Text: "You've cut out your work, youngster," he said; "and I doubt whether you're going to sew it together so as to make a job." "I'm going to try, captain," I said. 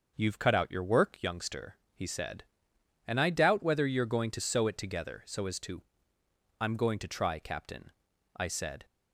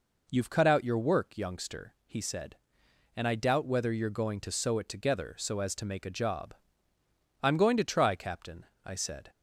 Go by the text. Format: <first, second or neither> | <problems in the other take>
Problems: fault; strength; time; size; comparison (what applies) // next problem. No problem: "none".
second | starts louder than the rest; noticeable; until 1.1 s; 6 dB // skips "make a job"; at 6.2 s